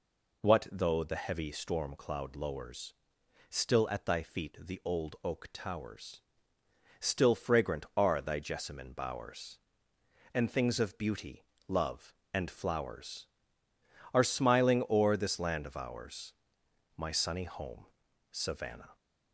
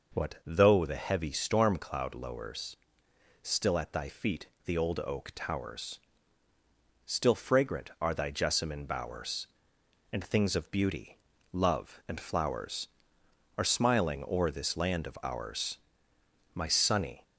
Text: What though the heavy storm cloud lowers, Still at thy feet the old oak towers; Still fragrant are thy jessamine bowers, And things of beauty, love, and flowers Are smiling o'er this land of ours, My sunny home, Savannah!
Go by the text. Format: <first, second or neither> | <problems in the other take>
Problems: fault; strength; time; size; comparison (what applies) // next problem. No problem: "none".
first | pauses between "feet" and "the"; slight; at 4.4 s; 0.20 s long // stops before "home Savannah"; at 17.2 s